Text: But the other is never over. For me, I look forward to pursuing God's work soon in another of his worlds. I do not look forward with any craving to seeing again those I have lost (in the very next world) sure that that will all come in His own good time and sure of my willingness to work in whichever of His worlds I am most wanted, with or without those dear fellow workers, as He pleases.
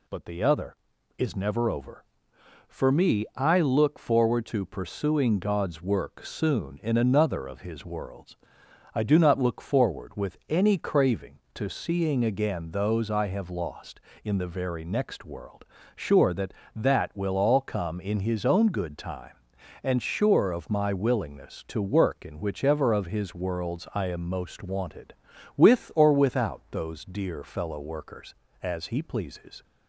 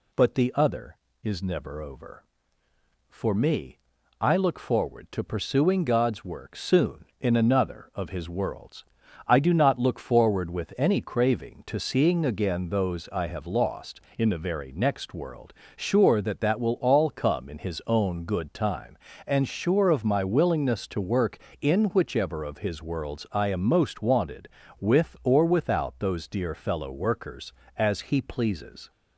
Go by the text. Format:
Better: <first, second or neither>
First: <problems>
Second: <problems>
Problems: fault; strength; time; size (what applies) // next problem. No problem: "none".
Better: neither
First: none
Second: none